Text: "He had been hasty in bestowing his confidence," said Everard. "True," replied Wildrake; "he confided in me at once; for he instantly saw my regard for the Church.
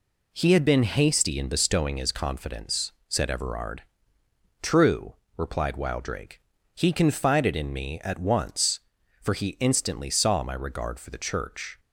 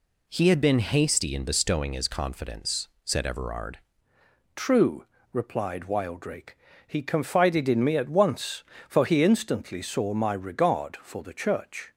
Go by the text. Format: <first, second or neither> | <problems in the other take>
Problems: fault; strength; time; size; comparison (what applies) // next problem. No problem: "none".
first | changes voice at "True"; from 4.5 s on; 7.4 s long